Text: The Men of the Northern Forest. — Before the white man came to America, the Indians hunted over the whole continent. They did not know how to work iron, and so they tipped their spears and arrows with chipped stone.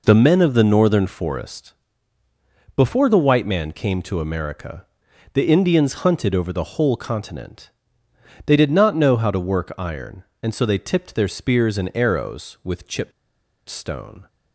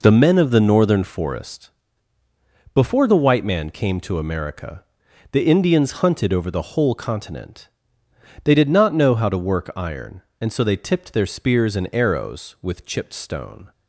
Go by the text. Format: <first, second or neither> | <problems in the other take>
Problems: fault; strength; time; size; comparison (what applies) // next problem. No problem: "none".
second | pauses between "chipped" and "stone"; noticeable; at 13.1 s; 0.57 s long